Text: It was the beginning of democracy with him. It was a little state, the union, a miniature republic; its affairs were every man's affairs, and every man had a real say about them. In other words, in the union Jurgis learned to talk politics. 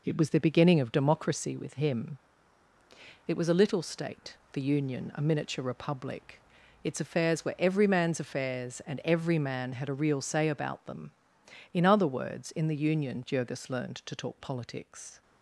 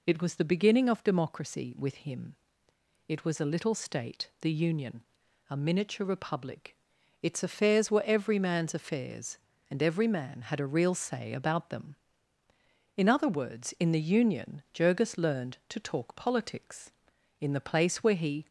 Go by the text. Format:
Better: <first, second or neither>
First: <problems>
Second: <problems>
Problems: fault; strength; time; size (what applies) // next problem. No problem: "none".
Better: first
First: none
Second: goes on to say "In the place where he"; noticeable; from 17.3 s on; 1.0 s long